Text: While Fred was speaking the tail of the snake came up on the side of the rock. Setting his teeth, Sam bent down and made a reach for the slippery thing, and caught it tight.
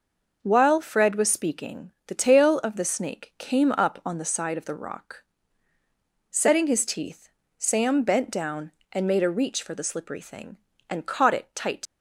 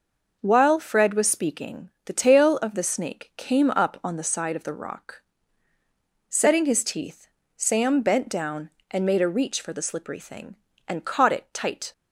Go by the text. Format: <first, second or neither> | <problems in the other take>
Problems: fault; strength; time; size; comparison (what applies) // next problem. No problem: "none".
second | leaves "tight" unfinished; at 11.8 s; 85 ms